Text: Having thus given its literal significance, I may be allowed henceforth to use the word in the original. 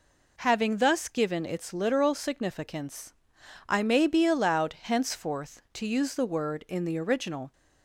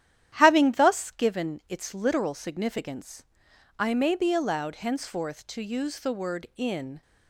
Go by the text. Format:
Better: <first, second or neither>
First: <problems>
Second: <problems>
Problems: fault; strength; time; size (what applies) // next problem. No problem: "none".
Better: first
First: none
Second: starts louder than the rest; strong; until 1.3 s; 11 dB // stops before "the original"; at 7.0 s